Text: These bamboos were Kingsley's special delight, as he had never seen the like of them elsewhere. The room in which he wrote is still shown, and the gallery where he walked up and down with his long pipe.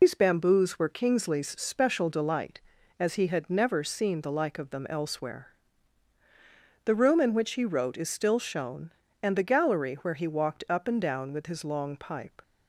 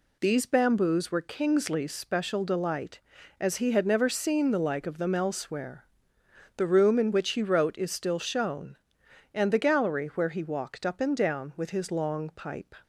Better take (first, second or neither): second